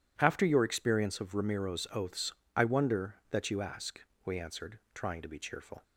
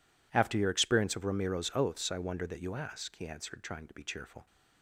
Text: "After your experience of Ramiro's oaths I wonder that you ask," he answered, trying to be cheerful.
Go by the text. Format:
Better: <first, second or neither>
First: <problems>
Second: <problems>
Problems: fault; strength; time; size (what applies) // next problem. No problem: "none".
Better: second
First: pauses between "oaths" and "I"; slight; at 2.3 s; 0.24 s long // says "we" for "he"; at 4.2 s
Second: none